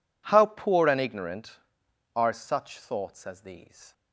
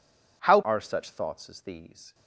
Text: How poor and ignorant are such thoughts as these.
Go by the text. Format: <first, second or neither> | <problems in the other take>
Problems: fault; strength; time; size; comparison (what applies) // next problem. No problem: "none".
first | skips "poor and ignorant"; at 0.6 s